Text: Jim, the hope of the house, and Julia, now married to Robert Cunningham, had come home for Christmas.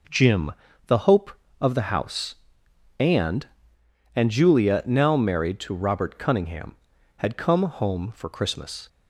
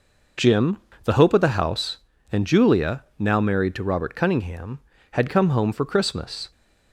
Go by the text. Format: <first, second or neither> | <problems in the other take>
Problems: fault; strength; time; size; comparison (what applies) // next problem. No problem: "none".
second | says "and" twice; at 4.1 s